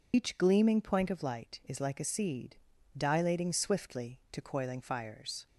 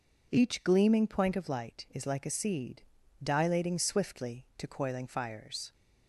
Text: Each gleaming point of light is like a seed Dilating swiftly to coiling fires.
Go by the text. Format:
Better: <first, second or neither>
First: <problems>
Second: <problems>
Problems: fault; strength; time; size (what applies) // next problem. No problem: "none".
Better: second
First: loses the start of "Each"; at 0.1 s; 90 ms // pauses between "seed" and "Dilating"; at 2.5 s; 0.38 s long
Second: pauses between "seed" and "Dilating"; at 2.8 s; 0.38 s long